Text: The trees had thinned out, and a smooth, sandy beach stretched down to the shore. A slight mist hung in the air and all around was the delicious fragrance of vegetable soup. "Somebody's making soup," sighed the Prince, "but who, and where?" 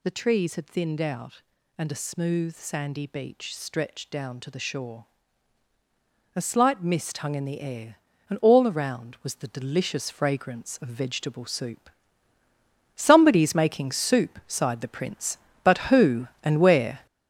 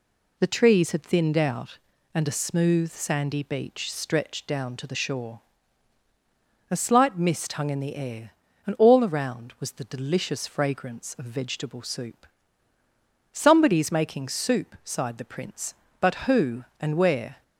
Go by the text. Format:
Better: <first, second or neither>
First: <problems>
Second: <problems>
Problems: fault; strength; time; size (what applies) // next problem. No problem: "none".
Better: second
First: gets louder; throughout; 6.5 dB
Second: none